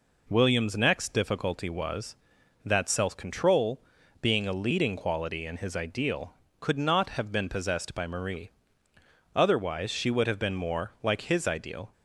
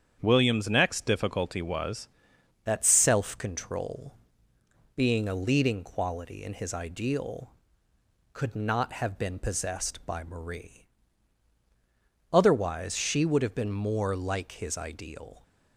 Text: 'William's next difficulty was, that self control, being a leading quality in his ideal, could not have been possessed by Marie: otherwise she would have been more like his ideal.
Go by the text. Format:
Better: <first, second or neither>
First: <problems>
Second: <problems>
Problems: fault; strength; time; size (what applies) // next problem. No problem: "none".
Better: first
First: none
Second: starts louder than the rest; strong; until 1.2 s; 8 dB // changes voice at "that"; from 2.6 s on; 12.8 s long